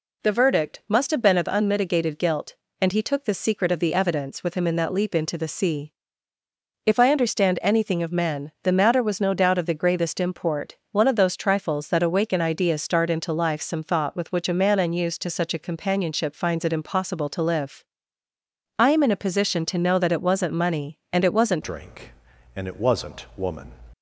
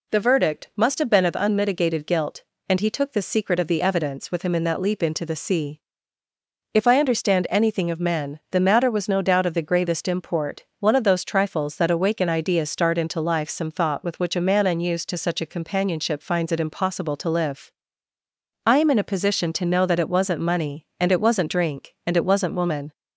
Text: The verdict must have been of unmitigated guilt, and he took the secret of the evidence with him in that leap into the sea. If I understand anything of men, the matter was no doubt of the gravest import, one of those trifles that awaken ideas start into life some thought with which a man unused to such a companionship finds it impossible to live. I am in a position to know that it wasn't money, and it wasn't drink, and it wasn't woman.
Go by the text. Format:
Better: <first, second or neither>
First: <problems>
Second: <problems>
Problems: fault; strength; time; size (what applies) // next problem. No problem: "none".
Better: second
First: changes voice at "drink"; from 21.6 s on; 2.1 s long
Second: none